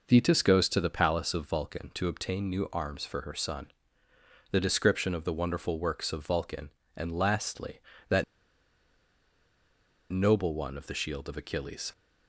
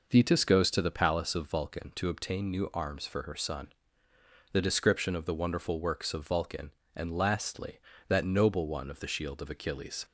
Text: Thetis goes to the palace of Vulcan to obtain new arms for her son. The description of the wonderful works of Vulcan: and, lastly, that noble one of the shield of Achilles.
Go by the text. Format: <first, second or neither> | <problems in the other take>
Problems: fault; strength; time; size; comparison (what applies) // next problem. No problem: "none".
second | pauses between "that" and "noble"; strong; at 8.2 s; 1.8 s long